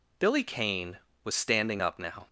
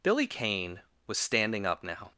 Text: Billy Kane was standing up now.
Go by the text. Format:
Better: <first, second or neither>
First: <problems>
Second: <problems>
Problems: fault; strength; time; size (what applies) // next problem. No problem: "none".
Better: neither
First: none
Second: none